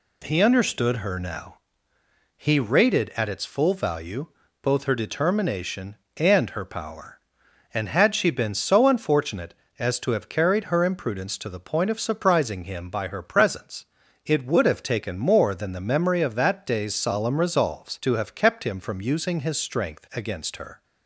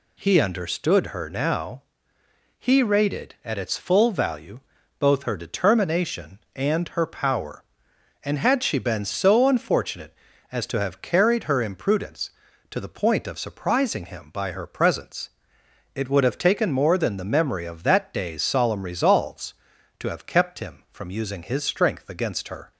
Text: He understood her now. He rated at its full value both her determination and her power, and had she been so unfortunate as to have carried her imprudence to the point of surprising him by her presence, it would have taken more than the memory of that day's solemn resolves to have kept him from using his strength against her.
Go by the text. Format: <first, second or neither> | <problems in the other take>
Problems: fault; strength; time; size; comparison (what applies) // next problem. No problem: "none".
neither | pauses between "value" and "both"; slight; the same in both